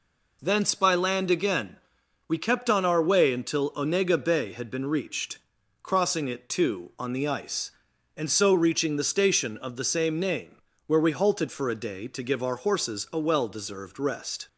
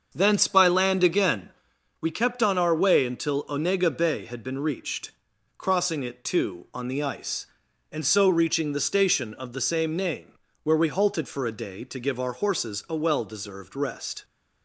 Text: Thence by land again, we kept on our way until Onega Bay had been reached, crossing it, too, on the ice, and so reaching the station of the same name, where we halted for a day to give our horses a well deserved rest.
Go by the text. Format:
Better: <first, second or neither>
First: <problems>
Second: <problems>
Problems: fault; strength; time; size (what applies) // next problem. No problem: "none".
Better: first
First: none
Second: starts louder than the rest; until 1.8 s; 6.5 dB